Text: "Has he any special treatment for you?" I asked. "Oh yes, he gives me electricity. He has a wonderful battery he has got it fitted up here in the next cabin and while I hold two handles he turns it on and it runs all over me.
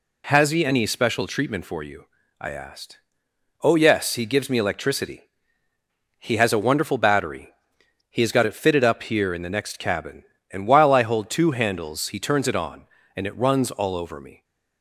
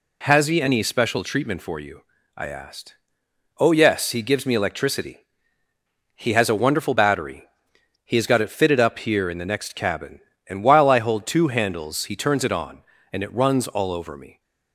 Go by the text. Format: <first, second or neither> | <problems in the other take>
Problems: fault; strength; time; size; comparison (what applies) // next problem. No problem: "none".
neither | pauses between "battery" and "he"; noticeable; the same in both